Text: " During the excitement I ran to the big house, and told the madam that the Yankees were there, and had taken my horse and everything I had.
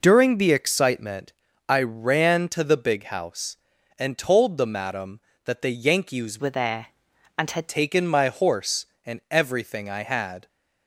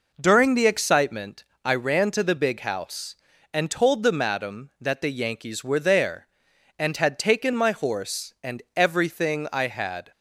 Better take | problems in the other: second | pauses between "excitement" and "I"; at 1.3 s; 0.38 s long; slight in the second // changes voice from "were" to "had"; from 6.3 to 7.6 s; 1.3 s long

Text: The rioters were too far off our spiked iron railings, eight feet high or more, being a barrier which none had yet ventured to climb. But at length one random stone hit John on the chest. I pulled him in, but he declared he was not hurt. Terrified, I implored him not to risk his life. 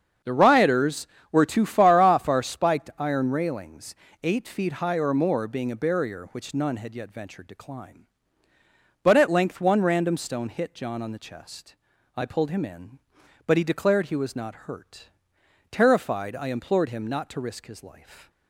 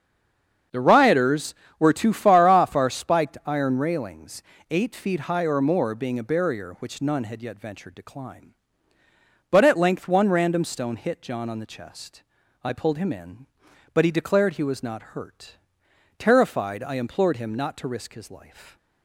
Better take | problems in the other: first | stays silent before the first word; slight; until 0.7 s; 0.7 s long // starts louder than the rest; until 1.9 s; 7 dB; also in the first

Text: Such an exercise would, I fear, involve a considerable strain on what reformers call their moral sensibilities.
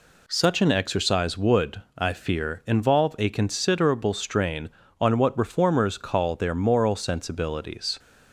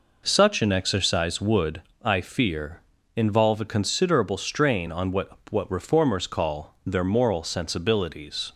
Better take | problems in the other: first | says "what" twice; at 5.4 s

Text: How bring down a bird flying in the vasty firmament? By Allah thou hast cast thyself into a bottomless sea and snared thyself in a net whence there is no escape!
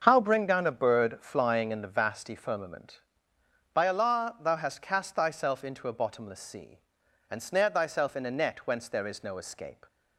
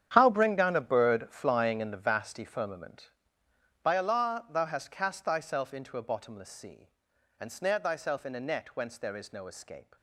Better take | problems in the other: first | gets quieter; strong; throughout; 14.5 dB // starts louder than the rest; strong; until 1.1 s; 9.5 dB; also in the first

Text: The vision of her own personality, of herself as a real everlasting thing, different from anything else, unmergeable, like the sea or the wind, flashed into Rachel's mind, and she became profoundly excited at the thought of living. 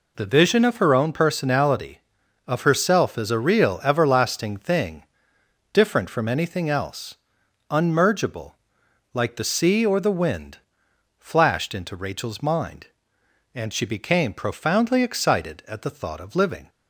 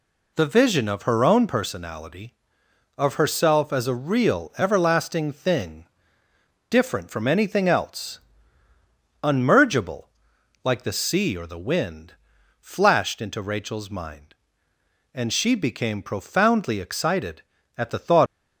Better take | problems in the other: first | stops before "of living"; at 18.2 s

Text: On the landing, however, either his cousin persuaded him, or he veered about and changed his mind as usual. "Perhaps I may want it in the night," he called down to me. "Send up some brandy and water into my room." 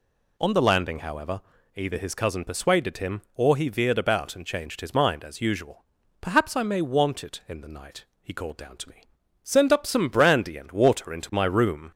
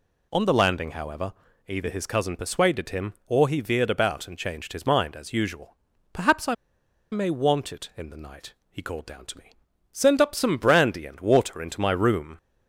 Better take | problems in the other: first | pauses between "I" and "may"; noticeable; at 6.5 s; 0.57 s long

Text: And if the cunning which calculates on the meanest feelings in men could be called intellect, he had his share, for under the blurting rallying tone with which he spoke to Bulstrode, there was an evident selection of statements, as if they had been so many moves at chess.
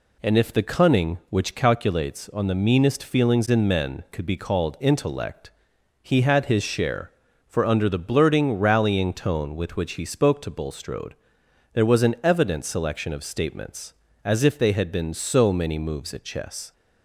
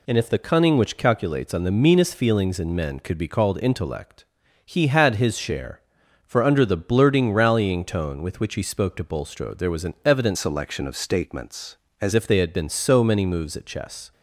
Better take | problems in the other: first | changes voice from "selection" to "as"; from 10.3 to 12.1 s; 1.8 s long

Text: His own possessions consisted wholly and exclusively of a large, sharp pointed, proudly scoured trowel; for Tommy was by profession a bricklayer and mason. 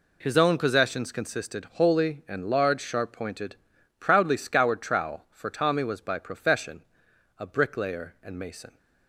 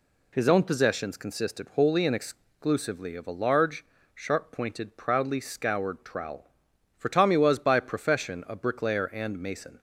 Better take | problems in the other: second | skips "exclusively of a"; at 2.4 s // pauses between "profession" and "a"; noticeable; at 6.8 s; 0.54 s long

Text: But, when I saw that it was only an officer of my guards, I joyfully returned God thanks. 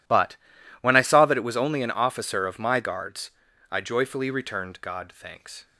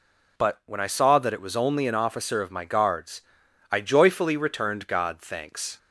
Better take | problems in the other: neither | none

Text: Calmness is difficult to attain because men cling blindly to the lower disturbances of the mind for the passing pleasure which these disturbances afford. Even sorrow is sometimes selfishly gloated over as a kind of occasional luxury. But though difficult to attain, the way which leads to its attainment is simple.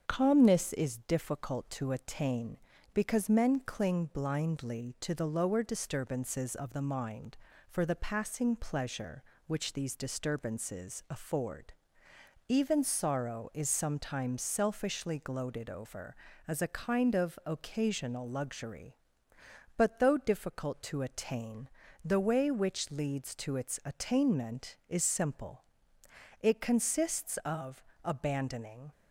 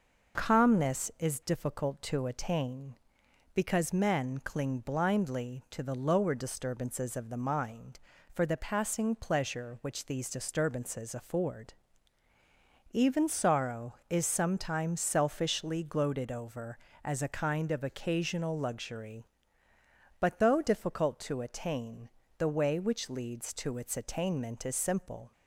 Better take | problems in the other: second | starts louder than the rest; until 1.0 s; 7 dB // goes on to say "It consists of abandoning"; strong; from 26.4 s on; 2.4 s long

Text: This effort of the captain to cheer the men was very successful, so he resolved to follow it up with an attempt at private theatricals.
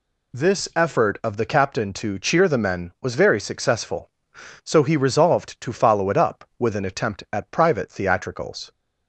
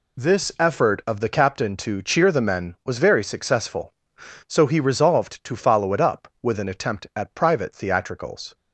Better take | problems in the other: first | gets quieter; strong; throughout; 9 dB

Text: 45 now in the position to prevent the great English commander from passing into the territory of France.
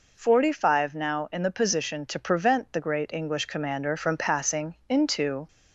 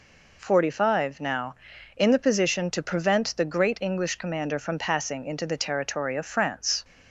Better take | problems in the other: second | stops before "the territory of France"; at 5.4 s

